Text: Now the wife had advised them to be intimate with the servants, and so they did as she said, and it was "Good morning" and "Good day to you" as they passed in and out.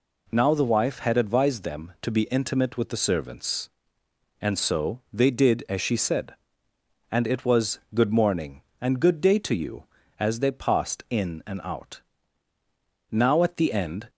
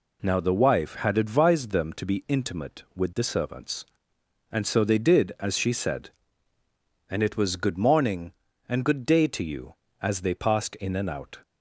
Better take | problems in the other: second | pauses between "was" and "Good"; slight; at 7.7 s; 0.16 s long // goes on to say "Now at the end"; noticeable; from 13.0 s on; 1.0 s long

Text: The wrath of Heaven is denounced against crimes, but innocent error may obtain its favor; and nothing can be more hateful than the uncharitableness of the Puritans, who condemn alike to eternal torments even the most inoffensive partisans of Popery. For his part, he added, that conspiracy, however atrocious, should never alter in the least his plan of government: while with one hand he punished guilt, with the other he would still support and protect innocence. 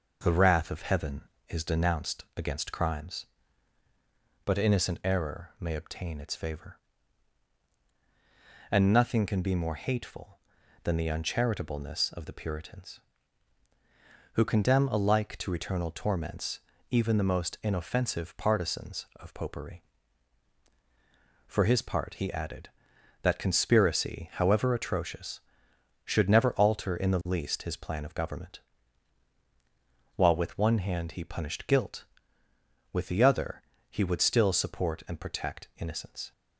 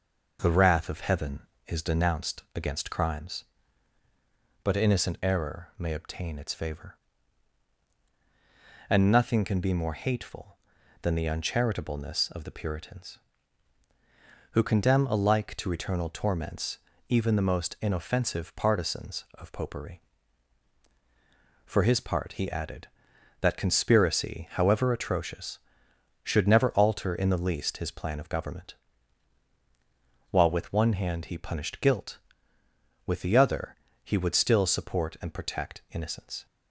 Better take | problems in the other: neither | pauses between "torments" and "even"; slight; the same in both // pauses between "other" and "he"; slight; the same in both

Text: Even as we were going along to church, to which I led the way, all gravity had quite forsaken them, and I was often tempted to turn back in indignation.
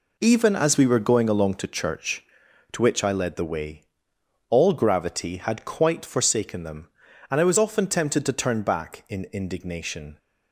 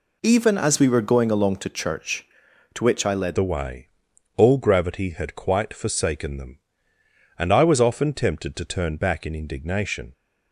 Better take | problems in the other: first | changes voice at "the"; from 3.3 s on; 6.8 s long

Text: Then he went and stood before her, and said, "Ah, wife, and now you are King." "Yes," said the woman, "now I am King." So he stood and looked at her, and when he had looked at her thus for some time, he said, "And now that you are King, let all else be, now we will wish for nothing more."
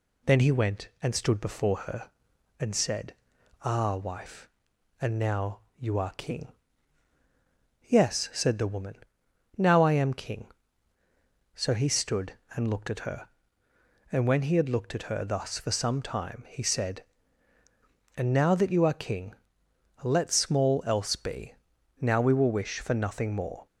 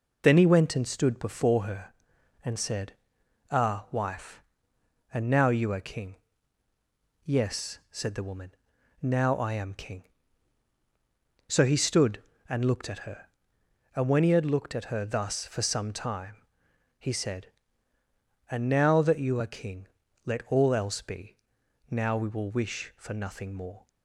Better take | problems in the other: second | pauses between "now" and "you"; slight; at 5.6 s; 0.18 s long // says "small" for "all"; at 20.3 s

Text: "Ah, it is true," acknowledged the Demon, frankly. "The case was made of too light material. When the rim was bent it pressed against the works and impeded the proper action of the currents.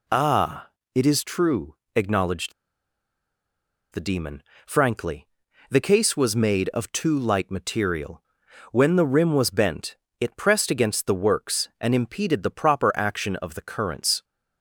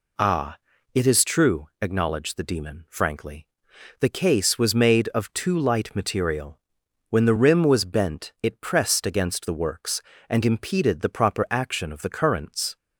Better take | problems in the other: second | pauses between "acknowledged" and "the"; strong; at 2.5 s; 1.4 s long // pauses between "bent" and "it"; slight; at 9.9 s; 0.22 s long

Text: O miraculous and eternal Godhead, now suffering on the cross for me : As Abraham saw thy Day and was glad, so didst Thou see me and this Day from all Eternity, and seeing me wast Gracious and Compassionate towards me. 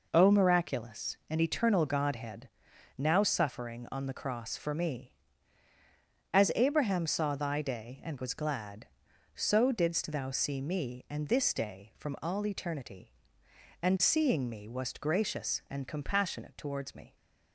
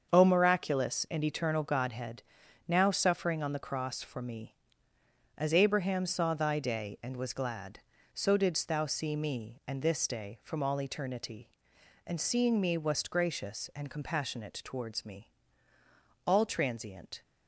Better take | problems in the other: first | starts louder than the rest; until 1.1 s; 7 dB // goes on to say "All transient"; noticeable; from 16.2 s on; 0.98 s long

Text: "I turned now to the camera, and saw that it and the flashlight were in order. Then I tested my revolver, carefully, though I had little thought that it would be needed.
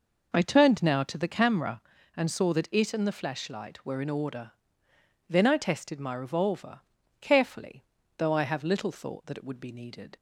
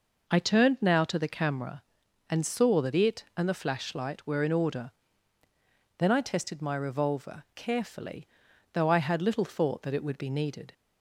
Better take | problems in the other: second | says "have" for "had"; at 8.4 s

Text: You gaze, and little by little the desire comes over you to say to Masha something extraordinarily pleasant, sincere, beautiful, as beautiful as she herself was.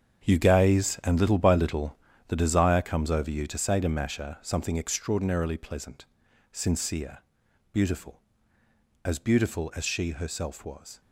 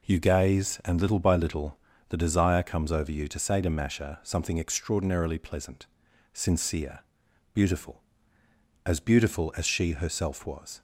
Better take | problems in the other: second | gets quieter; strong; throughout; 11.5 dB // pauses between "little" and "the"; slight; at 1.9 s; 0.32 s long; slight in the second

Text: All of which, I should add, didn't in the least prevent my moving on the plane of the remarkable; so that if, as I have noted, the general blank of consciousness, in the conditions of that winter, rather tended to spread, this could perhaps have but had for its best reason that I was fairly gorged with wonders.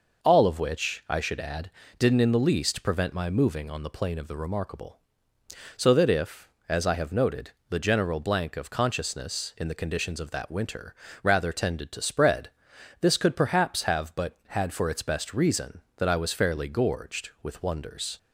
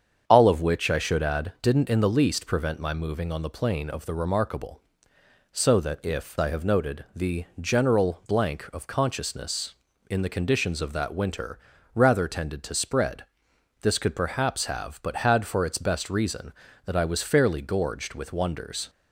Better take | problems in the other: first | starts louder than the rest; strong; until 1.2 s; 7.5 dB // skips "as"; at 6.3 s

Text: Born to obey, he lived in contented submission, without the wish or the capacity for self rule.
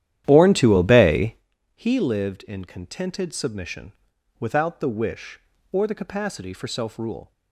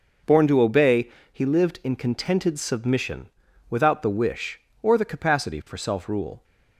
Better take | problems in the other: second | starts louder than the rest; strong; until 1.4 s; 11.5 dB

